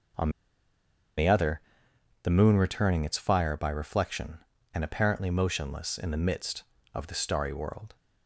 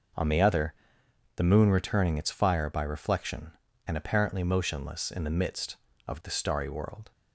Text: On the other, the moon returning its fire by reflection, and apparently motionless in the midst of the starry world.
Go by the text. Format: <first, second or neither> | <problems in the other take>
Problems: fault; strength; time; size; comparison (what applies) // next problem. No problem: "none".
second | pauses between "On" and "the"; noticeable; at 0.2 s; 0.88 s long